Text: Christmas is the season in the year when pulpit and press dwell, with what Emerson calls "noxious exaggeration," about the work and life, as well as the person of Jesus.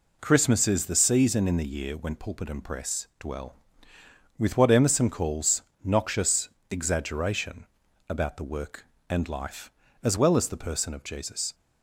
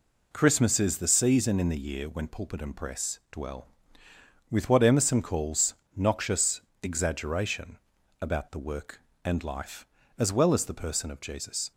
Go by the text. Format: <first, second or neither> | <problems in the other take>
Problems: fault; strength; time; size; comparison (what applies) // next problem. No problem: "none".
neither | pauses between "calls" and "noxious"; slight; the same in both // pauses between "noxious" and "exaggeration"; slight; the same in both